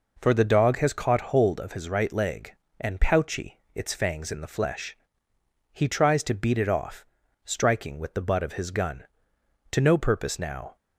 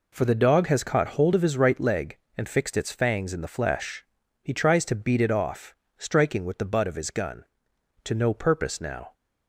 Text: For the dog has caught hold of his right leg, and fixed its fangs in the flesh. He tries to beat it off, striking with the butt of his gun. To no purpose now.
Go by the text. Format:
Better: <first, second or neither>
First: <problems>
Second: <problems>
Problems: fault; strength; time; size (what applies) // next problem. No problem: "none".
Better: second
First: says "pouchy" for "fixed"; at 3.0 s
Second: none